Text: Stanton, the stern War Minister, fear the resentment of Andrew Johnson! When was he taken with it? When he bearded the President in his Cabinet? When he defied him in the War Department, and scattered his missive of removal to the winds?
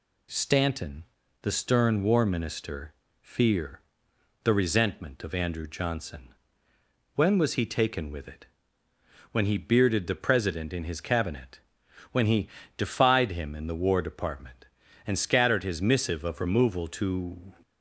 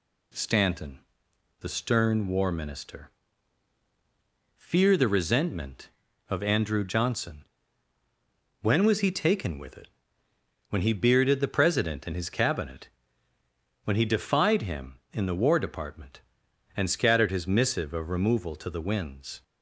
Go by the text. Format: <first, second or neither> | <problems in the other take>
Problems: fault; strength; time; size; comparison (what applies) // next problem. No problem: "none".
second | pauses between "fear" and "the"; noticeable; at 3.8 s; 0.62 s long // pauses between "he" and "defied"; slight; at 12.4 s; 0.30 s long // stops before "the winds"; at 17.6 s